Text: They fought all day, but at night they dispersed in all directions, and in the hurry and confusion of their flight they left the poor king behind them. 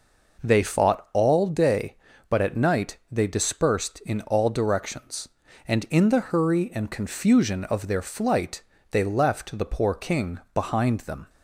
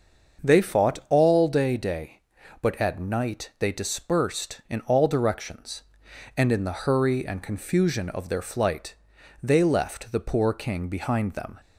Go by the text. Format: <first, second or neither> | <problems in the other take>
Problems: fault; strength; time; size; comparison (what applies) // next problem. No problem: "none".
first | starts louder than the rest; until 1.5 s; 6.5 dB // says "day" twice; at 1.7 s // pauses between "flight" and "they"; noticeable; at 8.9 s; 0.48 s long; slight in the first